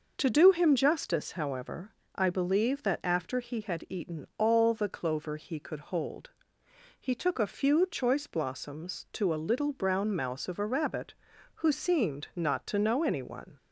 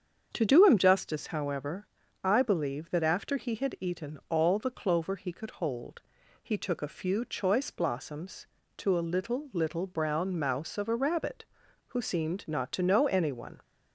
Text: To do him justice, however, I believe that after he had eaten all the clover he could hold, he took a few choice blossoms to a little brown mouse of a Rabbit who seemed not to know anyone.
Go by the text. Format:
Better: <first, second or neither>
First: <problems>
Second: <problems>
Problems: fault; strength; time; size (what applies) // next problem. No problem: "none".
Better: first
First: none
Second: starts louder than the rest; strong; until 1.3 s; 7.5 dB // says "little" twice; at 9.5 s